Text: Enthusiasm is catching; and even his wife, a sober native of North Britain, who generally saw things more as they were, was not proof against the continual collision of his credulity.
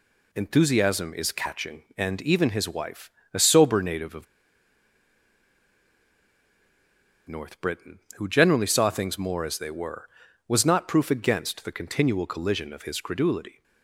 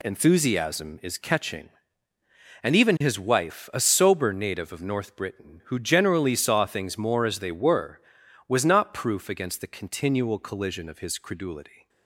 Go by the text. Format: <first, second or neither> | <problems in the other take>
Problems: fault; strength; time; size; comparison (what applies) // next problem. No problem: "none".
second | pauses between "of" and "North"; strong; at 4.2 s; 3.0 s long